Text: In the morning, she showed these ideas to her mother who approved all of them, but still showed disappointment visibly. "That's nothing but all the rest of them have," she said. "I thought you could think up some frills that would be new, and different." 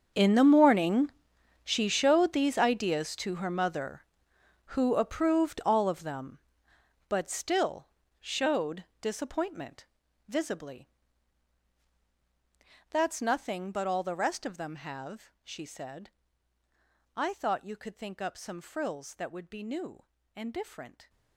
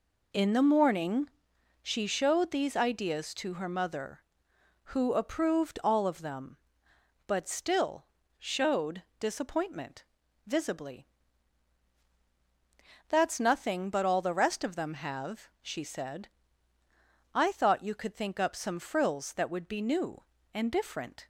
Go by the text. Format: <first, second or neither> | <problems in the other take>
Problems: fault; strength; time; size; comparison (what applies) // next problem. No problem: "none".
second | gets quieter; strong; throughout; 18 dB // pauses between "still" and "showed"; slight; at 7.8 s; 0.32 s long; slight in the second // pauses between "showed" and "disappointment"; slight; at 8.8 s; 0.16 s long; slight in the second // pauses between "disappointment" and "visibly"; at 9.8 s; 0.42 s long; also in the second